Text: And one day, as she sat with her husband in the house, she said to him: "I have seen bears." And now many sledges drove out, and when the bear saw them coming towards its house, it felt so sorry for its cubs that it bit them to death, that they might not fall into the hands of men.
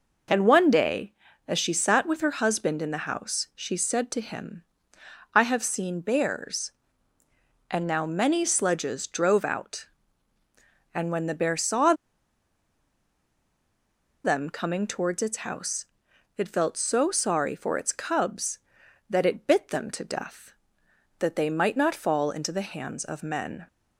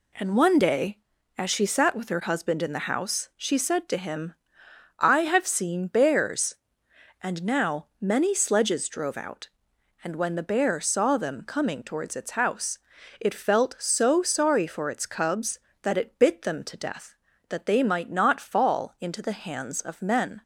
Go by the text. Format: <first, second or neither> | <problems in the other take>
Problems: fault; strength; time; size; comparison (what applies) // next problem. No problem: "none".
second | pauses between "saw" and "them"; strong; at 11.9 s; 2.2 s long